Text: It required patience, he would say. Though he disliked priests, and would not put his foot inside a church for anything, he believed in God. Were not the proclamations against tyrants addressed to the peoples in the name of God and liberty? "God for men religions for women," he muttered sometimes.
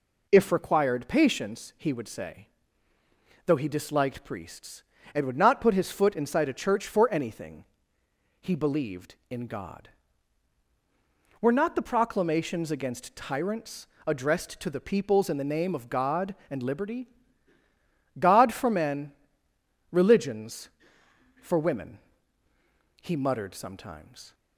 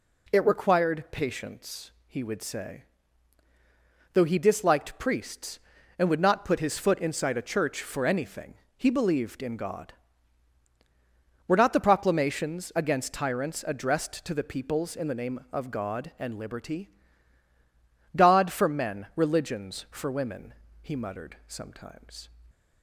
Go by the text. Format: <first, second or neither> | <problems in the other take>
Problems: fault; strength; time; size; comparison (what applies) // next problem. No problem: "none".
second | says "If" for "It"; at 0.2 s // pauses between "tyrants" and "addressed"; slight; at 13.8 s; 0.20 s long // pauses between "men" and "religions"; noticeable; at 19.1 s; 0.80 s long